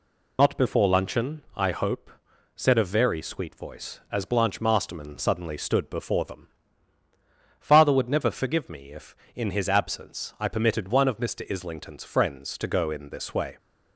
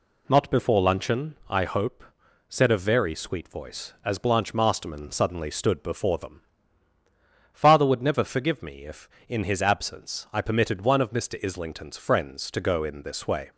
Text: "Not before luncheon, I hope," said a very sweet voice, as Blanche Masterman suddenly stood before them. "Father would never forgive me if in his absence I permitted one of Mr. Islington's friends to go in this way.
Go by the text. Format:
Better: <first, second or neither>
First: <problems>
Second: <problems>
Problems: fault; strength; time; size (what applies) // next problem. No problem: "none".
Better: second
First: loses the start of "Not"; at 0.3 s; 55 ms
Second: none